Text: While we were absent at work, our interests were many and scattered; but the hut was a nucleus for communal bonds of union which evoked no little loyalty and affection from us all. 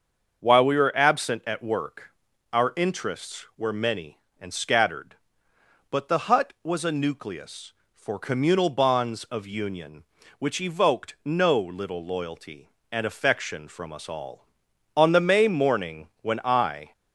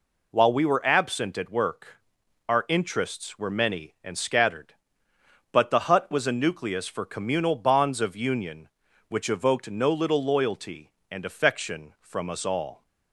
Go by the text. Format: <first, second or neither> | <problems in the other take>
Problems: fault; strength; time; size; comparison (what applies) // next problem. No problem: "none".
second | starts louder than the rest; until 1.4 s; 6.5 dB // goes on to say "On the May morning when I"; strong; from 14.9 s on; 1.9 s long